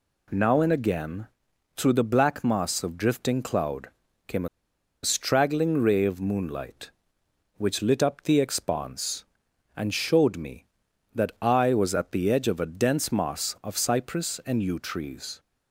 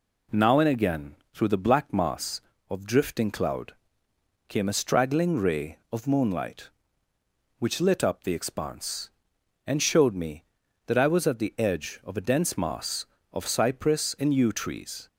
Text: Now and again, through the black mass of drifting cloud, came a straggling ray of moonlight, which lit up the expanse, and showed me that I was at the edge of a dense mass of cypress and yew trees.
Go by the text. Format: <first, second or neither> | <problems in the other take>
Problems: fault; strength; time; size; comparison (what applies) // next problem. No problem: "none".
second | pauses between "a" and "straggling"; noticeable; at 4.4 s; 0.57 s long